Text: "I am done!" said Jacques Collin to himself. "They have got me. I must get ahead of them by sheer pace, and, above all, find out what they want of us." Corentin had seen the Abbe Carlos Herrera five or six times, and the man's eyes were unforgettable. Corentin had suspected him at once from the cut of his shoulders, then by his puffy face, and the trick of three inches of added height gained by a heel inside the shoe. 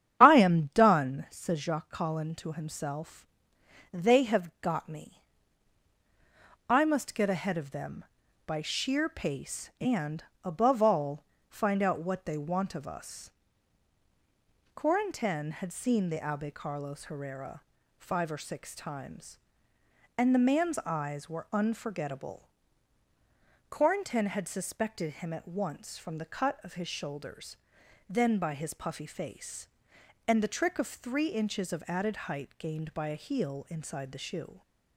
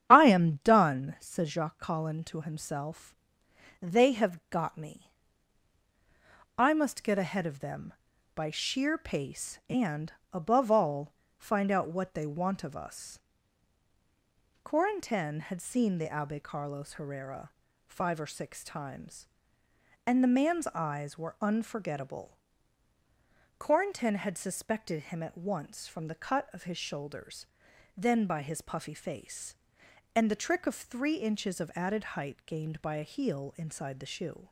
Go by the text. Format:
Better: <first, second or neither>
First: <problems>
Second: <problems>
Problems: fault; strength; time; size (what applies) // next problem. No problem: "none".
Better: neither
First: starts louder than the rest; strong; until 1.2 s; 9.5 dB // pauses between "Herrera" and "five"; at 17.6 s; 0.38 s long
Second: starts louder than the rest; strong; until 1.1 s; 9.5 dB // pauses between "Herrera" and "five"; at 17.4 s; 0.38 s long